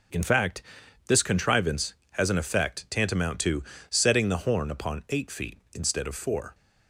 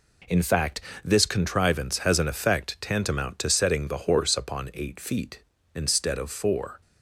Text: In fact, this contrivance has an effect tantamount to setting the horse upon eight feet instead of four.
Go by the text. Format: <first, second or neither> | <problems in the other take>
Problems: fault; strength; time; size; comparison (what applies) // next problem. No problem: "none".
second | pauses between "to" and "setting"; slight; at 3.6 s; 0.26 s long // says "horn" for "horse"; at 4.3 s